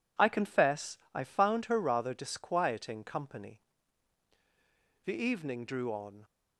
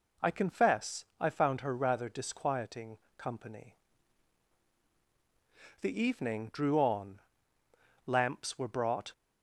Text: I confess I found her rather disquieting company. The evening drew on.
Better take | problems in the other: first | pauses between "confess" and "I"; slight; at 1.0 s; 0.16 s long; slight in the first // pauses between "disquieting" and "company"; slight; at 2.9 s; 0.22 s long // goes on to say "Lamps were brought"; noticeable; from 8.0 s on; 1.0 s long

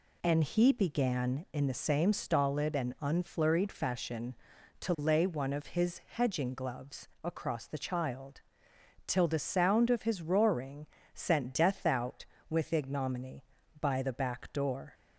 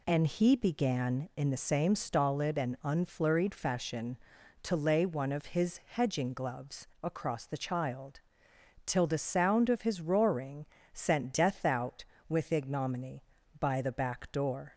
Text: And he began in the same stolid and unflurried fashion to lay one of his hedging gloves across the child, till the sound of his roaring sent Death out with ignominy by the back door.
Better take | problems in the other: neither | pauses between "gloves" and "across"; slight; the same in both // pauses between "roaring" and "sent"; slight; the same in both

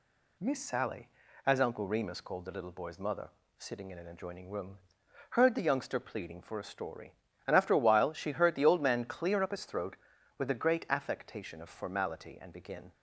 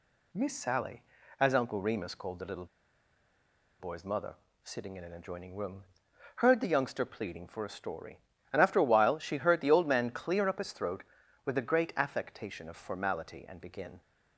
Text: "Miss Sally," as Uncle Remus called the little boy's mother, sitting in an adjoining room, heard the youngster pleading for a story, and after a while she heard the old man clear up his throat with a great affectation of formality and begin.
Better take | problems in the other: first | pauses between "little" and "boy's"; at 2.6 s; 1.1 s long

